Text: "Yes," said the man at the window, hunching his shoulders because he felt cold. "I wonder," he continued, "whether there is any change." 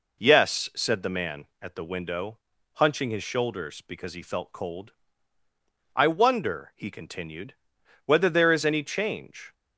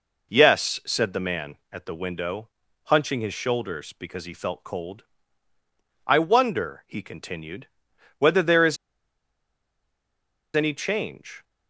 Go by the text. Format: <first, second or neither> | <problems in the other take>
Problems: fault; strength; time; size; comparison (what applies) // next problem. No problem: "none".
first | pauses between "is" and "any"; strong; at 8.7 s; 1.7 s long